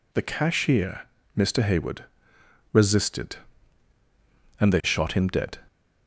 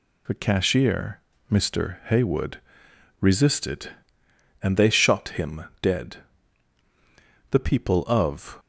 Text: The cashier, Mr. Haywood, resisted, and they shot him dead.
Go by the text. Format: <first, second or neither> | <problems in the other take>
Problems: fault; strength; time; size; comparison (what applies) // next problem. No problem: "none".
first | goes on to say "The people of"; noticeable; from 7.5 s on; 1.0 s long